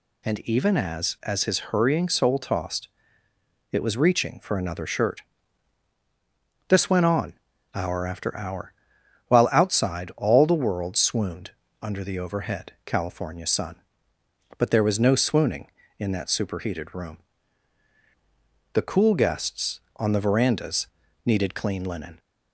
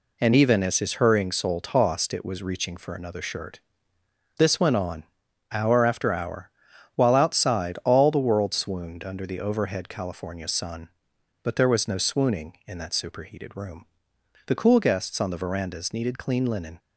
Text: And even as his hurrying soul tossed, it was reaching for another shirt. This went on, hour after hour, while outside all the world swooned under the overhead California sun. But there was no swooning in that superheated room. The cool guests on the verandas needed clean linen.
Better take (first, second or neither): second